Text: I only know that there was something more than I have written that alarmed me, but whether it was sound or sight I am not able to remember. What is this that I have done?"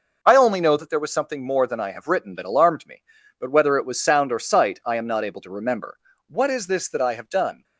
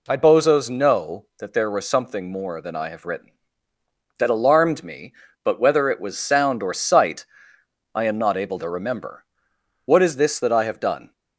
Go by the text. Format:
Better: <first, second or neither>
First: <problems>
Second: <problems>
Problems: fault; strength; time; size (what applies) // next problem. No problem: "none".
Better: first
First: none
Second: says "bozos" for "only"; at 0.1 s // pauses between "sight" and "I"; noticeable; at 7.2 s; 0.70 s long